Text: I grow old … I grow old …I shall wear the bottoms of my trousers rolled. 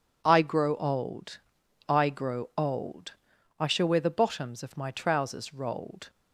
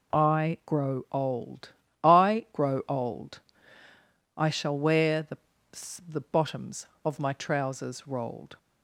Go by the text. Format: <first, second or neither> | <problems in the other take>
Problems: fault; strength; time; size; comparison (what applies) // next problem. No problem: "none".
first | says "the" twice; at 6.0 s